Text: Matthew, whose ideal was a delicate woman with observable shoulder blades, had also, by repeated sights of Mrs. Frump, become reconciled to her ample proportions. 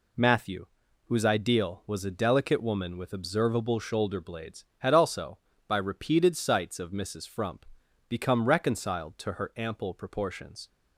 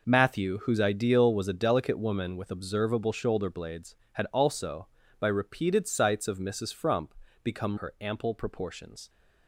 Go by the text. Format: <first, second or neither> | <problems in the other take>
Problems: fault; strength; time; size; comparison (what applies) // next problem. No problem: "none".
first | skips "reconciled to"; at 7.7 s